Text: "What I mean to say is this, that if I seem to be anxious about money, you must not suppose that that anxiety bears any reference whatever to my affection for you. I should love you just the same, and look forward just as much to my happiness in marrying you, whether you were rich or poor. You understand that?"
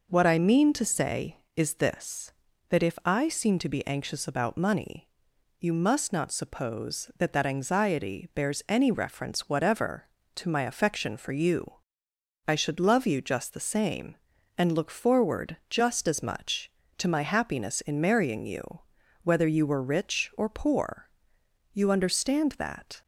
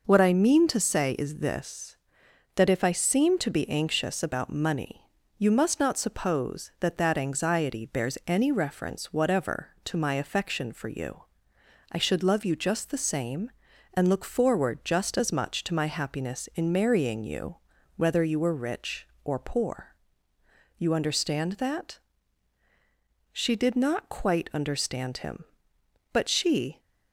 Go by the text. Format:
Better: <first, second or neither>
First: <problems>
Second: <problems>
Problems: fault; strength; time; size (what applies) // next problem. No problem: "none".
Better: first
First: none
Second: goes on to say "She did not quite understand him but she"; strong; from 23.3 s on; 3.4 s long